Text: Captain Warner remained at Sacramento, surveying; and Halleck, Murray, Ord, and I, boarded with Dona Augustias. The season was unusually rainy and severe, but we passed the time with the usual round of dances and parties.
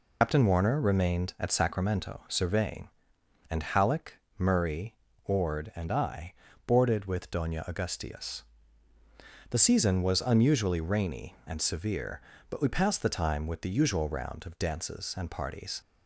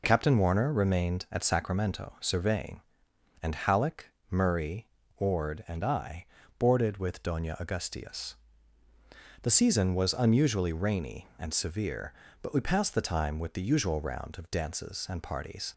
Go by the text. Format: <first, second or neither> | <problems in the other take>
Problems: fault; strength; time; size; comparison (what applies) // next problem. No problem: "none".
second | loses the start of "Captain"; at 0.2 s; 95 ms